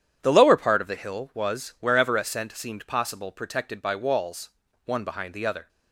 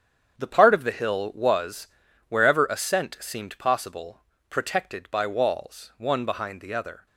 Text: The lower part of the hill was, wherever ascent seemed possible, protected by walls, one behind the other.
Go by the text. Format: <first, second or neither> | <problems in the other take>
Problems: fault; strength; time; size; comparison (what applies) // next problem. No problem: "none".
first | starts louder than the rest; strong; until 1.4 s; 8 dB; strong in the first // skips "lower"; at 0.4 s